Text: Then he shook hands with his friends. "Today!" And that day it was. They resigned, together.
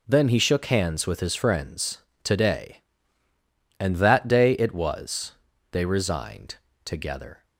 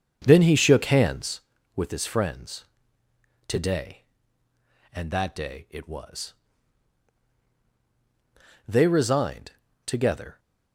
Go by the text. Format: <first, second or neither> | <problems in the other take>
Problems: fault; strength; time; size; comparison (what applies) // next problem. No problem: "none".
first | starts louder than the rest; strong; until 1.2 s; 7 dB